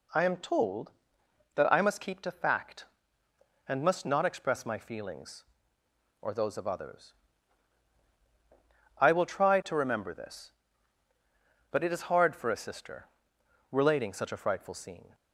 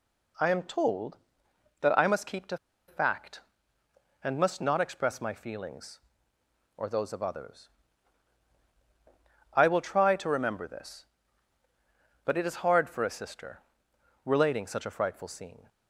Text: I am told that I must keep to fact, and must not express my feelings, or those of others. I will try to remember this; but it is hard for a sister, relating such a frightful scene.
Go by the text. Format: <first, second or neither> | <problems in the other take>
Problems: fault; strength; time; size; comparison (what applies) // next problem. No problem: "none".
first | pauses between "to" and "fact"; slight; at 2.5 s; 0.31 s long